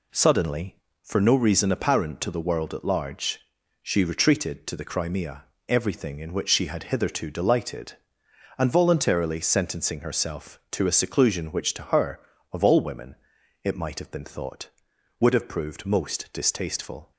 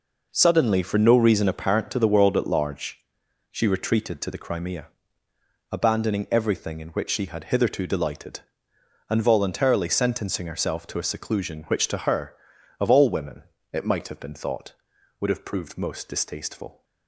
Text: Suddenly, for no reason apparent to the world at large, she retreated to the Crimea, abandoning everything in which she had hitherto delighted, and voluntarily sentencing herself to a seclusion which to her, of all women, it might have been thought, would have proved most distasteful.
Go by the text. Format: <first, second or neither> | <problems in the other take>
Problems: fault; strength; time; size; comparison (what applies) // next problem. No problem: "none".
second | skips "abandoning"; at 5.5 s